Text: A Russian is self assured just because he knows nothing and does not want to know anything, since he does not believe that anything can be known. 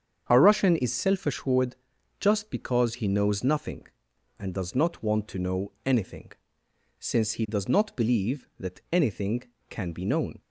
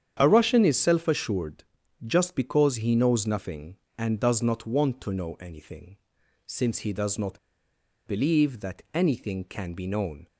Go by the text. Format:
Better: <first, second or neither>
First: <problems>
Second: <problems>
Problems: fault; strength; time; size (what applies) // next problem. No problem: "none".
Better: first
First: starts louder than the rest; strong; until 1.3 s; 7.5 dB // pauses between "assured" and "just"; at 1.7 s; 0.42 s long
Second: starts louder than the rest; strong; until 1.2 s; 9 dB // pauses between "assured" and "just"; at 1.6 s; 0.42 s long // pauses between "not" and "believe"; noticeable; at 7.3 s; 0.68 s long